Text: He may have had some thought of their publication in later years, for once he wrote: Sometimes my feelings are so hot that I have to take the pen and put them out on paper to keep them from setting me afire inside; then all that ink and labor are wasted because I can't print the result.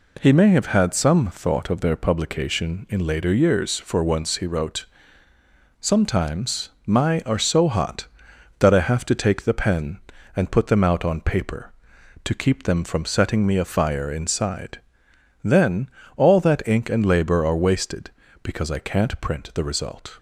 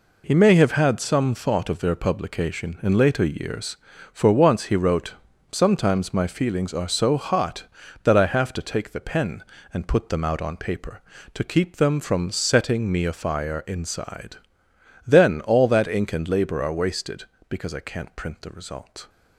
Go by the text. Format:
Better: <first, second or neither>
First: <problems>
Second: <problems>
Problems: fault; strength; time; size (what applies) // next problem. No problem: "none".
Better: second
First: pauses between "Sometimes" and "my"; slight; at 6.6 s; 0.18 s long // skips "feelings"; at 7.2 s // pauses between "then" and "all"; slight; at 15.8 s; 0.28 s long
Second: none